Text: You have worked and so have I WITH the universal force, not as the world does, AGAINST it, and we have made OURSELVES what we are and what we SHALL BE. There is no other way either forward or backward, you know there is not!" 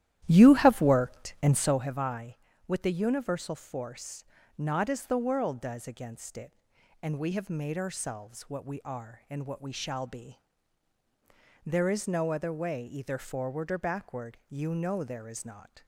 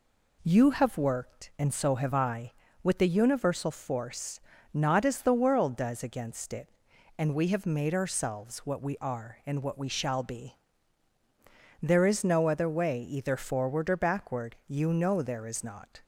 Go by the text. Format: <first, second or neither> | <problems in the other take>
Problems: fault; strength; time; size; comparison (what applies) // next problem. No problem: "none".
second | starts louder than the rest; strong; until 1.9 s; 12.5 dB